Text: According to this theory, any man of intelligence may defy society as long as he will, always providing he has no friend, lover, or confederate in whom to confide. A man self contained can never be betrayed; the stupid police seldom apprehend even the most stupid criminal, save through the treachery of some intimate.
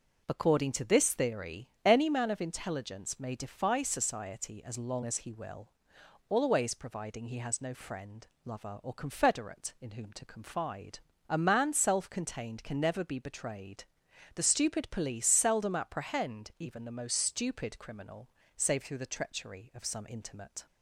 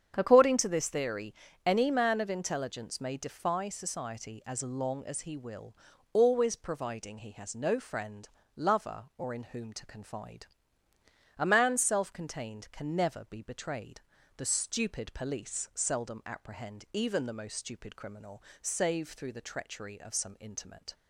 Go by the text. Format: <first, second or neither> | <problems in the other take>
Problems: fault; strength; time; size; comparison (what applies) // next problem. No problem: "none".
first | starts louder than the rest; strong; until 1.1 s; 8 dB; also in the first // skips "confederate"; at 9.3 s